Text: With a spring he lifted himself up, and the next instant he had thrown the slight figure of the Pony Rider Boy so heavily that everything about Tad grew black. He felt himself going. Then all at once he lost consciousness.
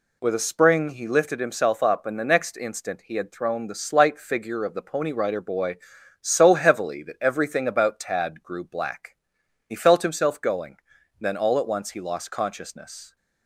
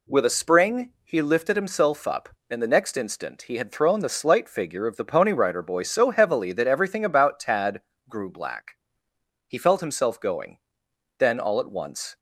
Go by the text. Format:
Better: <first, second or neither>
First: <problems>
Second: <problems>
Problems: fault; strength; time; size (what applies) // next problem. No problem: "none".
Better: first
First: none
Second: pauses between "Tad" and "grew"; slight; at 7.8 s; 0.26 s long // stops before "he lost consciousness"; at 12.1 s